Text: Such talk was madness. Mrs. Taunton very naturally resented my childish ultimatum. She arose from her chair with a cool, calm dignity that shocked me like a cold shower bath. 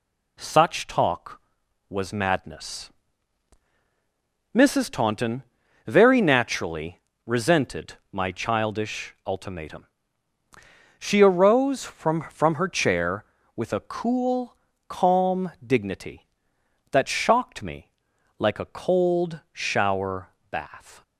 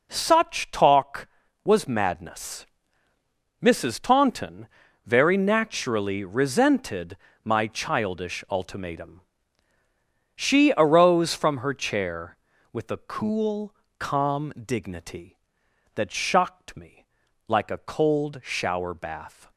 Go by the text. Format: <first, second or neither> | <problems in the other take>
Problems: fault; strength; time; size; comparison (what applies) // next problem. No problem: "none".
second | pauses between "Taunton" and "very"; at 5.4 s; 0.42 s long; also in the second // pauses between "naturally" and "resented"; slight; at 7.0 s; 0.26 s long // pauses between "resented" and "my"; slight; at 7.9 s; 0.18 s long; slight in the second // says "from" twice; at 12.3 s // pauses between "calm" and "dignity"; slight; at 15.5 s; 0.16 s long // pauses between "me" and "like"; noticeable; at 17.9 s; 0.48 s long; also in the second // pauses between "shower" and "bath"; slight; at 20.2 s; 0.24 s long